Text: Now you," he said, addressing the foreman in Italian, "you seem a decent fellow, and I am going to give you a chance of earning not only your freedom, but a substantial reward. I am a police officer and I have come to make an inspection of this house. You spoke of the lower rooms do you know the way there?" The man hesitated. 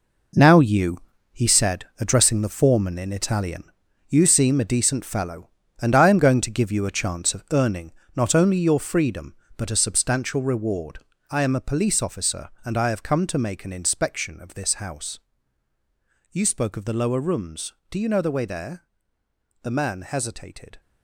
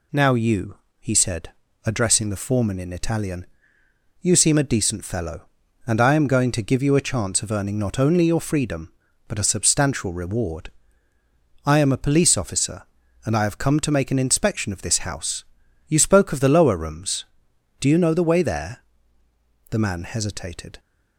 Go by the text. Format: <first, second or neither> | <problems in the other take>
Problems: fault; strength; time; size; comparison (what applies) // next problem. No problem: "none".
second | gets quieter; strong; throughout; 10.5 dB // pauses between "earning" and "not"; slight; at 7.9 s; 0.24 s long